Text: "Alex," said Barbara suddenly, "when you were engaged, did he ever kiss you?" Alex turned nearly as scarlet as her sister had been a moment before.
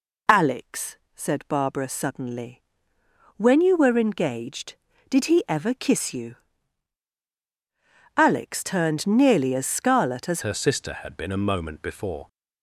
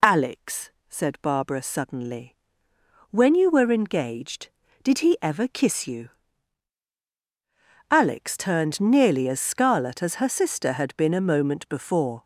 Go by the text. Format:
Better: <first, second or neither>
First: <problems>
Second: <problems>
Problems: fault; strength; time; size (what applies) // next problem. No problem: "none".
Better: second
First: changes voice at "her"; from 10.4 s on; 1.8 s long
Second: none